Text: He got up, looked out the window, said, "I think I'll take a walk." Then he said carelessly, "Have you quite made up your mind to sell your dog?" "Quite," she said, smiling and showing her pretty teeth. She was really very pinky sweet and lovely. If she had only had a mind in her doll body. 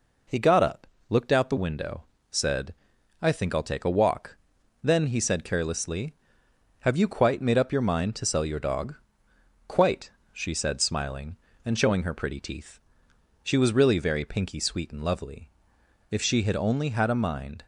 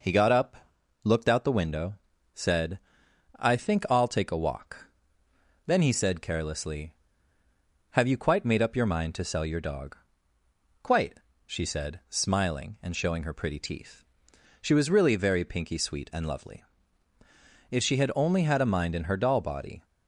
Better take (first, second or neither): second